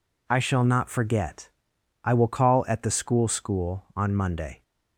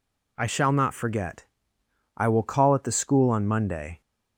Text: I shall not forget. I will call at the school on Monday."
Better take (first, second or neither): second